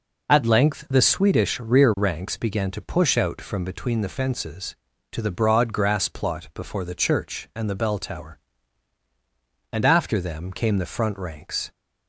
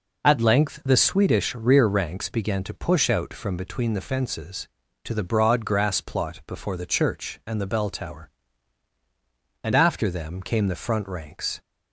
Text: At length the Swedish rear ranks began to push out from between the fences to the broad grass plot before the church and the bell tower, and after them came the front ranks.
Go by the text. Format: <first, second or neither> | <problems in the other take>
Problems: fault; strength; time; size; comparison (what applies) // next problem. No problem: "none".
neither | none